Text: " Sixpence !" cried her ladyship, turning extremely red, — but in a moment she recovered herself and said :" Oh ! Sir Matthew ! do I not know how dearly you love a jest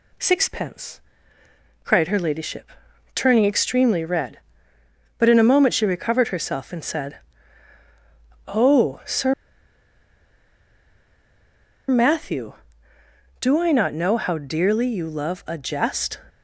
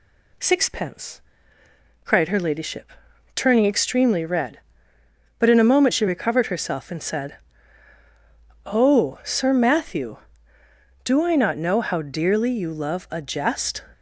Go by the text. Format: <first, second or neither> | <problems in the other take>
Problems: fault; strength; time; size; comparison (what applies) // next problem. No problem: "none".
second | pauses between "Sir" and "Matthew"; strong; at 9.3 s; 2.5 s long